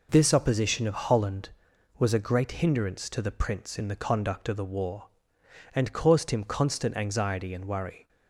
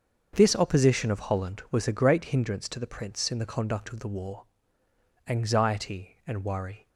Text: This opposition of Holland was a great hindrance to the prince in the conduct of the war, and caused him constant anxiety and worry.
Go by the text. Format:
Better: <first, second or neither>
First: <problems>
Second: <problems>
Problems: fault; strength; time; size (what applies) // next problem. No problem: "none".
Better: first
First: none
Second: starts louder than the rest; until 1.3 s; 6.5 dB // skips "and caused him constant"; at 4.8 s